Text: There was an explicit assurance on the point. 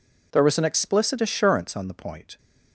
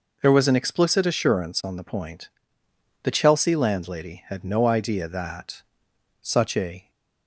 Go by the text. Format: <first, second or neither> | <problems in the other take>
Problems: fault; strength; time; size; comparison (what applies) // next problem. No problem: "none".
first | goes on to say "The Chelsea landlady had no idea that such a"; strong; from 3.0 s on; 3.8 s long